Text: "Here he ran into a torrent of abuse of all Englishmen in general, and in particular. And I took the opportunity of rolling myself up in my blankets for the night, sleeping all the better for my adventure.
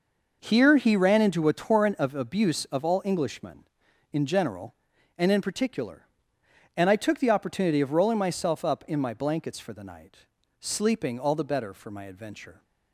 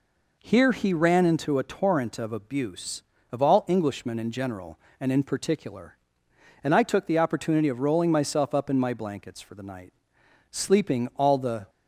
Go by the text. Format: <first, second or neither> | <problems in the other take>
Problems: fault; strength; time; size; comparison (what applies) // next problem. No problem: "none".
first | stops before "better for my adventure"; at 11.6 s